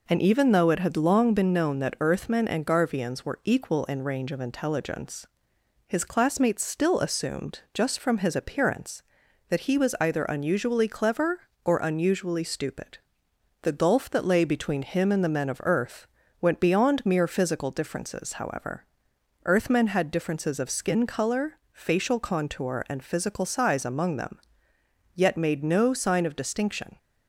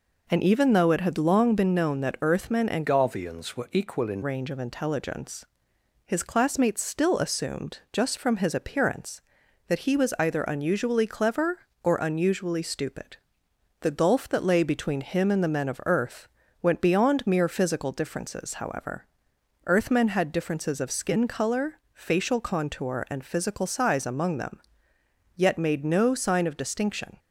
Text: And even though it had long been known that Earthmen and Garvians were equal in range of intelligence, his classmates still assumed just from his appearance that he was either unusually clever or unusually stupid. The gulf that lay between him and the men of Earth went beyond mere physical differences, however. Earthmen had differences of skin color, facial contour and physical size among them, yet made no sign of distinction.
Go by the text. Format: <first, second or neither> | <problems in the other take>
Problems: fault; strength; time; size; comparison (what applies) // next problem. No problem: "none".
first | changes voice from "Garvians" to "in"; from 2.8 to 4.2 s; 1.4 s long // pauses between "Earth" and "went"; slight; at 16.2 s; 0.36 s long; slight in the first